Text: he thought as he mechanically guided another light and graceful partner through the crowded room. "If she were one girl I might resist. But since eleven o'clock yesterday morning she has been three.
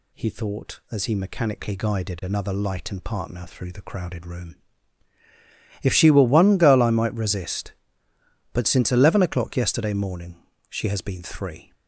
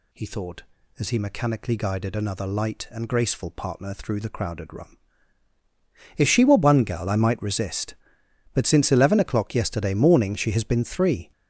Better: second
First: skips "graceful"; at 3.0 s // pauses between "morning" and "she"; slight; at 10.3 s; 0.34 s long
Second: none

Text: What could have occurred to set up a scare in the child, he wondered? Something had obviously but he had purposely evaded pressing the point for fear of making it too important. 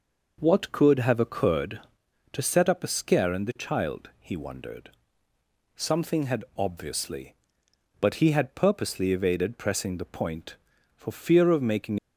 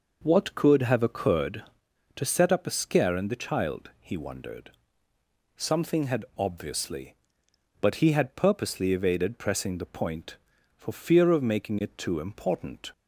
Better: second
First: stops before "it too important"; at 11.9 s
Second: none

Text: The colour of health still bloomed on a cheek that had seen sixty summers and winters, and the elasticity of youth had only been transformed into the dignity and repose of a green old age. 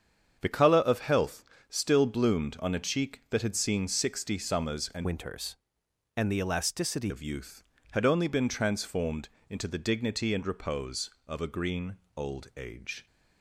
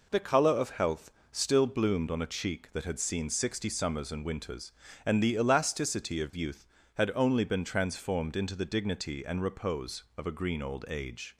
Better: second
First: starts louder than the rest; strong; until 1.4 s; 7.5 dB // pauses between "health" and "still"; slight; at 1.4 s; 0.24 s long // changes voice from "winters" to "elasticity"; from 5.0 to 7.1 s; 2.1 s long // pauses between "transformed" and "into"; slight; at 9.2 s; 0.22 s long // pauses between "green" and "old"; slight; at 11.9 s; 0.20 s long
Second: pauses between "health" and "still"; slight; at 1.1 s; 0.20 s long

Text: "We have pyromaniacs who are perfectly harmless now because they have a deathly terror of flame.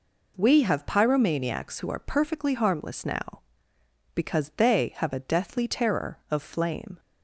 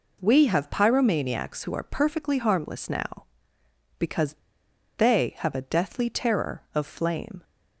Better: first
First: none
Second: pauses between "because" and "they"; noticeable; at 4.3 s; 0.62 s long

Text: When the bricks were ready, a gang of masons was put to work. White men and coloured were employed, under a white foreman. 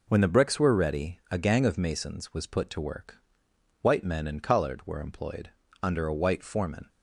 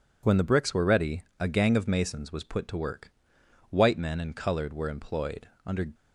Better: first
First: none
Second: stops before "a white foreman"; at 5.9 s

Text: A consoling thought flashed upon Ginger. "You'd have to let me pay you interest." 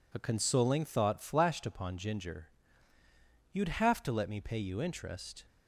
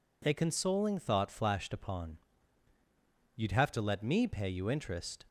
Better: first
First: none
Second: skips "Ginger"; at 2.7 s

